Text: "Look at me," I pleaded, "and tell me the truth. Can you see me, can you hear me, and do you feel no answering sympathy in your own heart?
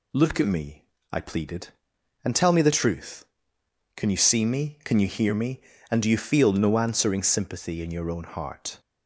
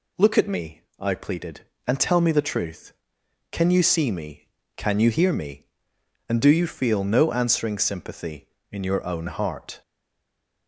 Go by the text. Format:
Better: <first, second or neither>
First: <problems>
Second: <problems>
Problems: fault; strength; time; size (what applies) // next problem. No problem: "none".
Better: first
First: none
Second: stays silent after the last word; slight; from 9.8 s on; 0.8 s long